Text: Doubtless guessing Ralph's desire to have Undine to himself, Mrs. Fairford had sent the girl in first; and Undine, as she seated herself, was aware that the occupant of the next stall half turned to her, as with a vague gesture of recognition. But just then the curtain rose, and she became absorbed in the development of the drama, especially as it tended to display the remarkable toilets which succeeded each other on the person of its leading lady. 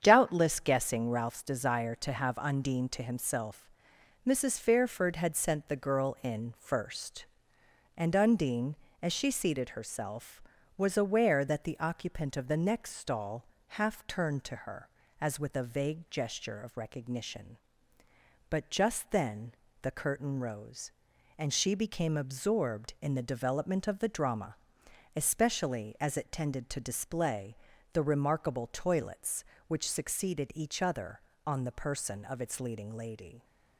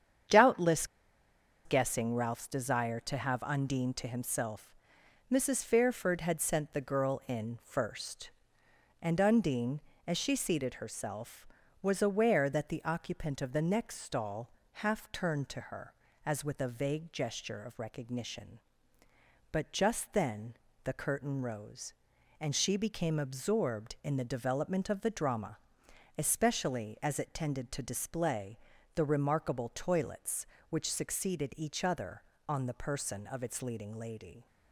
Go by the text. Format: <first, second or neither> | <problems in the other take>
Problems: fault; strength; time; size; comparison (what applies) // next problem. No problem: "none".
first | starts louder than the rest; strong; until 2.0 s; 8 dB; strong in the first // pauses between "Doubtless" and "guessing"; noticeable; at 0.8 s; 0.79 s long // pauses between "stall" and "half"; slight; at 14.4 s; 0.24 s long; slight in the first // pauses between "then" and "the"; slight; at 20.5 s; 0.30 s long; slight in the first // pauses between "display" and "the"; at 28.5 s; 0.38 s long; also in the first